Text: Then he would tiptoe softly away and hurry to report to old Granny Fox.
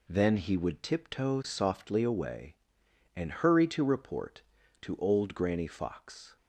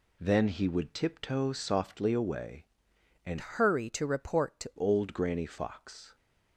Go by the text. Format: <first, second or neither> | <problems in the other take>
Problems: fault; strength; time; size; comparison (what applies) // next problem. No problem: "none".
first | changes voice from "hurry" to "to"; from 3.3 to 4.7 s; 1.4 s long